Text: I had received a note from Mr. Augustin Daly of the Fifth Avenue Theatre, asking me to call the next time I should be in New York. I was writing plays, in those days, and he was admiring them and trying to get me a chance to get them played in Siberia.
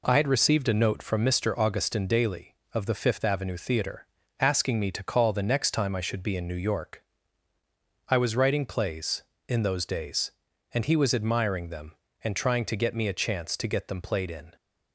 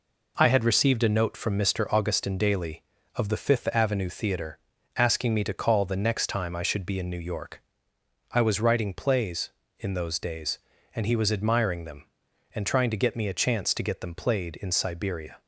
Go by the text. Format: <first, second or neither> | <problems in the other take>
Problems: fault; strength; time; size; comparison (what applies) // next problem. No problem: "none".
second | stops before "Siberia"; at 14.5 s